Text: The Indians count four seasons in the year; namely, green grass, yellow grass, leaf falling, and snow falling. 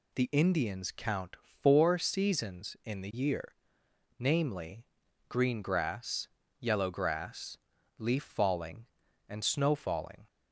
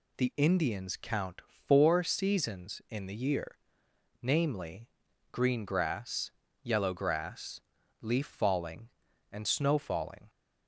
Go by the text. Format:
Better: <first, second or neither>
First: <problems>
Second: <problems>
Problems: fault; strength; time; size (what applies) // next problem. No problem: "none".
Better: neither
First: none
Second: none